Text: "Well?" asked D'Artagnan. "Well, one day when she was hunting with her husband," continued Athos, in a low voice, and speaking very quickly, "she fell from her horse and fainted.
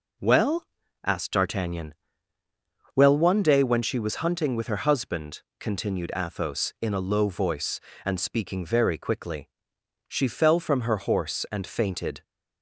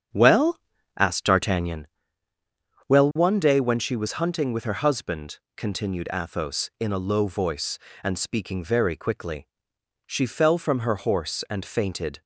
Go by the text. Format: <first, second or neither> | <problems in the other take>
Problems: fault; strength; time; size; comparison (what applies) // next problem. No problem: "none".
first | starts louder than the rest; strong; until 1.8 s; 8 dB